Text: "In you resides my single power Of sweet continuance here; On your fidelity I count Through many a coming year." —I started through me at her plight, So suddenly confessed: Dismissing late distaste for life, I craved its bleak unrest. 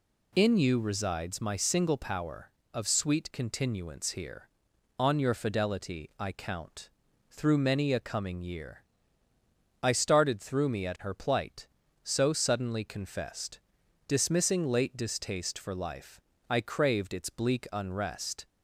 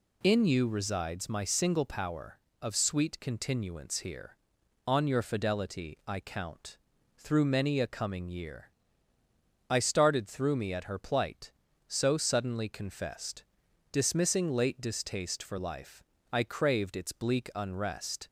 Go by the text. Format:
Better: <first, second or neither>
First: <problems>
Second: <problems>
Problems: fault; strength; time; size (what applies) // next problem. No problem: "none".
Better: neither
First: pauses between "count" and "Through"; at 6.8 s; 0.40 s long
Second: pauses between "count" and "Through"; at 6.7 s; 0.39 s long